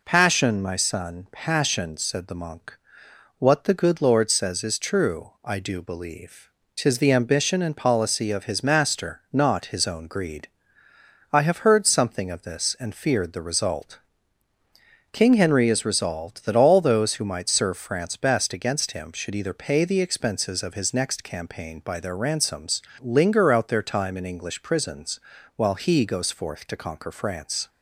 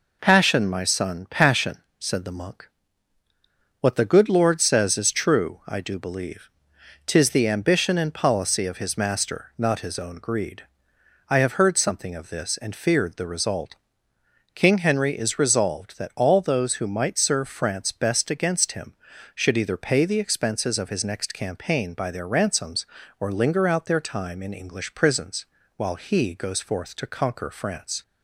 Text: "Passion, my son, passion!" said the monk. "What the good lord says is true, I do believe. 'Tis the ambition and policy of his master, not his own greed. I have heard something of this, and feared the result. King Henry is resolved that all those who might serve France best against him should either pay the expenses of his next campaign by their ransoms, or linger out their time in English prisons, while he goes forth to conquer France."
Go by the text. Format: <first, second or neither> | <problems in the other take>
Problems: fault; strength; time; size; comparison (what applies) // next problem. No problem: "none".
second | skips "or"; at 22.9 s